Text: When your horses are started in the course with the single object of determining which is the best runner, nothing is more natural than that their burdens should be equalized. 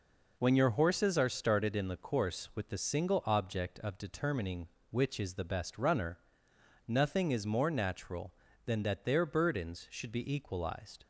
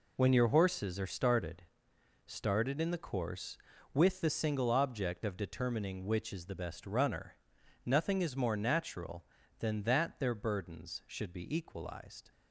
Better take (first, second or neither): first